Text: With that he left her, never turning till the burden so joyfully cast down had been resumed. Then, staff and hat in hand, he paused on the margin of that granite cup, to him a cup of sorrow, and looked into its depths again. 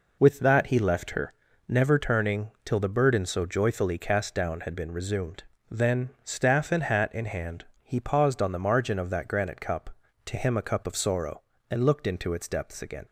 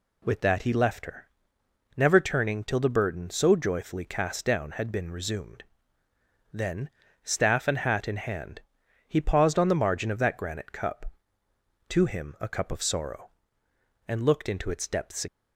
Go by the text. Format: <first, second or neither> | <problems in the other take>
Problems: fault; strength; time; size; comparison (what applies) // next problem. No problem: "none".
first | stops before "again"; at 15.2 s